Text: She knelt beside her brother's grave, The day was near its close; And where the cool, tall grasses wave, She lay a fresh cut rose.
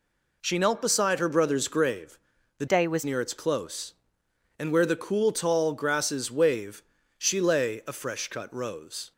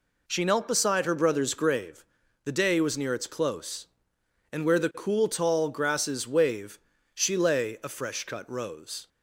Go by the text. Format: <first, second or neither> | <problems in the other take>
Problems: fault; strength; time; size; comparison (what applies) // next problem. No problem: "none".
second | changes voice from "day" to "was"; from 2.6 to 3.0 s; 0.4 s long